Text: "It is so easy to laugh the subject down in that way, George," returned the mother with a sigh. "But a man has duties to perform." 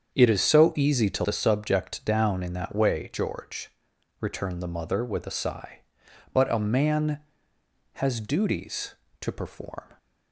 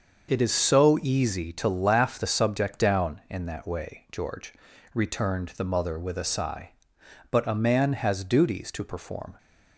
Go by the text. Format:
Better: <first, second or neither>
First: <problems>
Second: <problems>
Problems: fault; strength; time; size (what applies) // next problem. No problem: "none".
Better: second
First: starts louder than the rest; strong; until 1.1 s; 7.5 dB // skips "laugh"; at 1.2 s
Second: starts louder than the rest; until 1.3 s; 6.5 dB